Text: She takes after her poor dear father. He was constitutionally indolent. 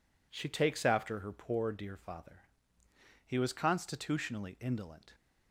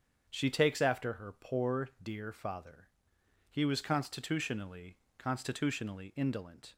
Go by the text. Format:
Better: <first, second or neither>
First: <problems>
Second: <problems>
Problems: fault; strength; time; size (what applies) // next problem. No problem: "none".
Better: first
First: none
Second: starts louder than the rest; strong; until 1.3 s; 7.5 dB // says "constitutionally" twice; at 5.1 s